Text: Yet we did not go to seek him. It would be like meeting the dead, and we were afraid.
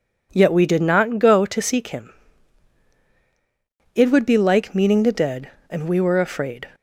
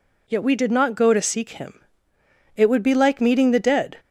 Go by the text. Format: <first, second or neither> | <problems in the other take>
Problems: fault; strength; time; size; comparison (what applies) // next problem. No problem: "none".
first | stops before "and we were afraid"; at 3.9 s